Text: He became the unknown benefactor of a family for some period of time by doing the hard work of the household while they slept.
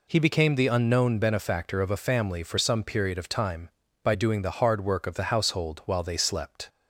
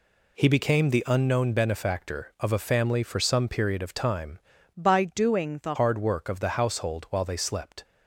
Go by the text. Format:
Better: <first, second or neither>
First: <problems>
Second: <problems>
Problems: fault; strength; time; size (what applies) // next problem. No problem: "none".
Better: first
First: none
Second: changes voice from "by" to "the"; from 4.7 to 5.7 s; 1.0 s long